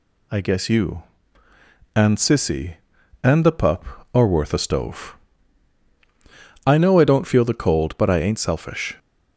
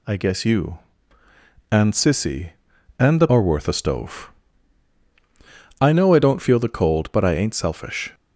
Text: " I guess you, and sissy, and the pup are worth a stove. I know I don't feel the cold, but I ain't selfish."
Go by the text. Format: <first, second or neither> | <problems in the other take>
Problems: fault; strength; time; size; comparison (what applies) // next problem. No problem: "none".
first | skips "pup"; at 3.2 s